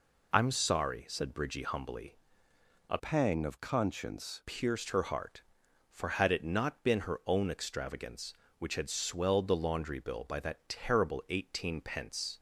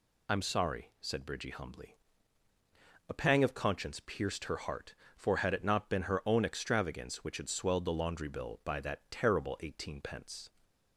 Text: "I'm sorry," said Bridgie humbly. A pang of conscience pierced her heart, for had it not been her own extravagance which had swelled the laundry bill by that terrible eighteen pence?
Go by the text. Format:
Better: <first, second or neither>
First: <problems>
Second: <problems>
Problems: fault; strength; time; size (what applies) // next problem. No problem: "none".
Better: second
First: changes voice from "pang" to "conscience"; from 2.9 to 4.4 s; 1.5 s long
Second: none